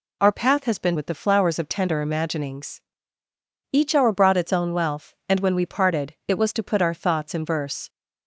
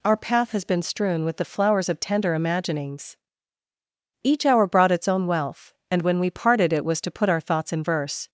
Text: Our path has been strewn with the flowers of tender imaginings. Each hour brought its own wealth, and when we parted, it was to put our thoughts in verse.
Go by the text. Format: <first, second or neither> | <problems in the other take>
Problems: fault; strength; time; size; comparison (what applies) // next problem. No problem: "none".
second | skips "strewn"; at 0.9 s